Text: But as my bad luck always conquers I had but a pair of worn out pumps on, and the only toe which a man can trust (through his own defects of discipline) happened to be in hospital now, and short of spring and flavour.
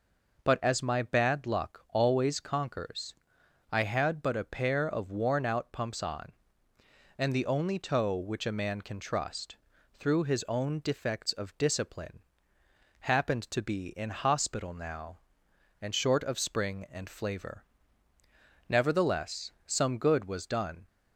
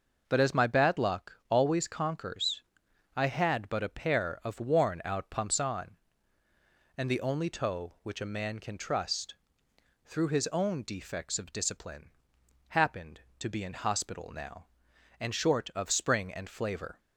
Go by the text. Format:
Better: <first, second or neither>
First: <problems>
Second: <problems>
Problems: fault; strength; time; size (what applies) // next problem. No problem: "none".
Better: second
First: pauses between "conquers" and "I"; noticeable; at 3.1 s; 0.56 s long // goes on to say "Nevertheless some good was done"; strong; from 18.6 s on; 2.1 s long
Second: pauses between "conquers" and "I"; noticeable; at 2.6 s; 0.52 s long